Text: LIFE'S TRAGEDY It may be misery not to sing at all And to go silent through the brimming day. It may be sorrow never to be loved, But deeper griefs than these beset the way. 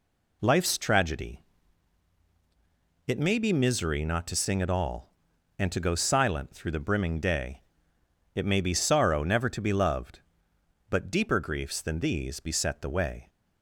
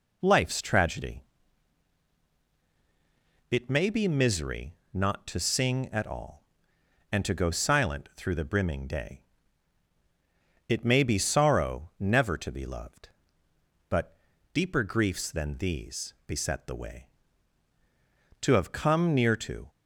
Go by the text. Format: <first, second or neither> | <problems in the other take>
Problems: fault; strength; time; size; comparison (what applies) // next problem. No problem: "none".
first | pauses between "TRAGEDY" and "It"; strong; at 1.2 s; 2.3 s long; strong in the first // pauses between "misery" and "not"; slight; at 4.7 s; 0.18 s long // pauses between "But" and "deeper"; at 14.1 s; 0.38 s long // goes on to say "To have come near to"; noticeable; from 18.4 s on; 1.2 s long